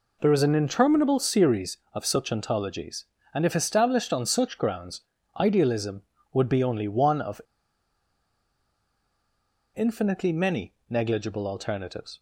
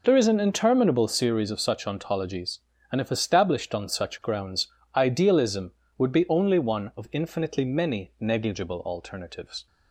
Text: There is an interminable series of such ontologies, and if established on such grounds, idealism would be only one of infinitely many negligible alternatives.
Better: second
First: pauses between "of" and "infinitely"; strong; at 7.4 s; 2.3 s long // pauses between "many" and "negligible"; slight; at 10.7 s; 0.16 s long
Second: none

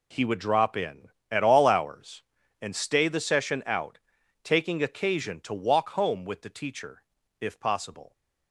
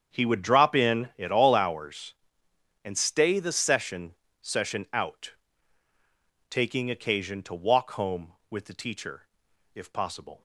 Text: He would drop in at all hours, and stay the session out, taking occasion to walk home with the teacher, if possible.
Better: first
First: none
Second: starts louder than the rest; strong; until 1.2 s; 7.5 dB // says "session" twice; at 4.4 s

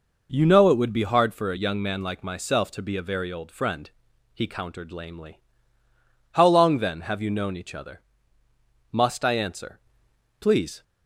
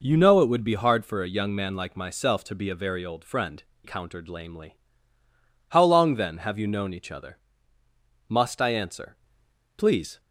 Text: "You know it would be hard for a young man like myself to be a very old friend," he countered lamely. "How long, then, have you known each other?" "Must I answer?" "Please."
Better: first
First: none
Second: skips "he"; at 3.7 s

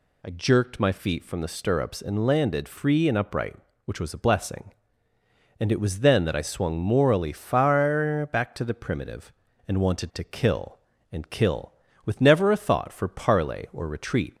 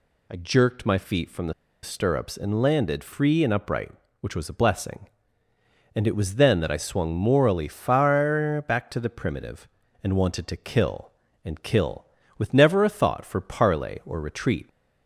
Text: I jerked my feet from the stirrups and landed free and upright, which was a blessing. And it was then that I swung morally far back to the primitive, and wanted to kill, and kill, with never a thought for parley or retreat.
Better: first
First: none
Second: pauses between "the" and "stirrups"; slight; at 1.5 s; 0.30 s long

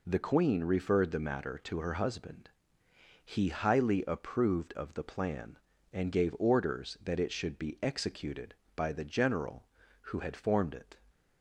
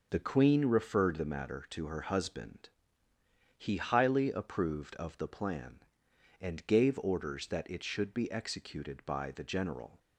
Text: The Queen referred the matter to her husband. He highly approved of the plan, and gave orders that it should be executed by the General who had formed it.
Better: first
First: none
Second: stops before "who had formed it"; at 9.9 s

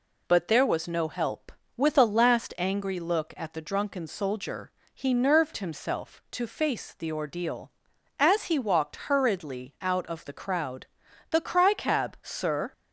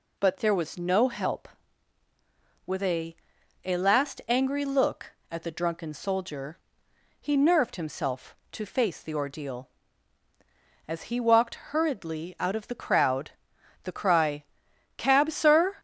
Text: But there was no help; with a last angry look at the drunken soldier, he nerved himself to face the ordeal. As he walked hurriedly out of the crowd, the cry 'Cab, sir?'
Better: first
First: none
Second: says "a" twice; at 3.6 s // pauses between "cry" and "Cab"; noticeable; at 14.4 s; 0.52 s long

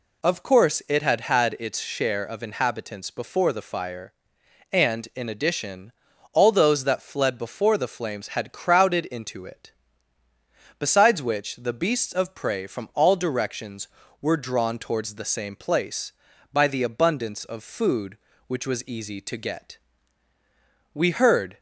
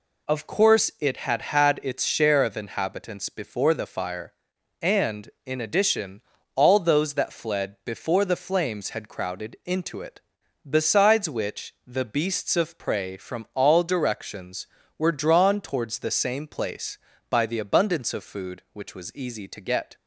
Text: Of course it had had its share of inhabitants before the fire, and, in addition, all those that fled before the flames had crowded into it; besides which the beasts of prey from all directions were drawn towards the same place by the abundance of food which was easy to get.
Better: second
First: goes on to say "We heard"; noticeable; from 20.9 s on; 0.66 s long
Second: none

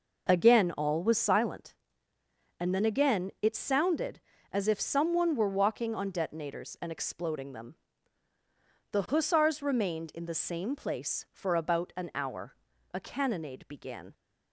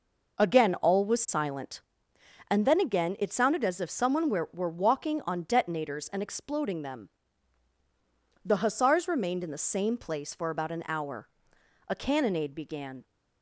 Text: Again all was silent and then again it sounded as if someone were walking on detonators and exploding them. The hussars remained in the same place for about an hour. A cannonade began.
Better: first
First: none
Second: says "were" twice; at 4.5 s

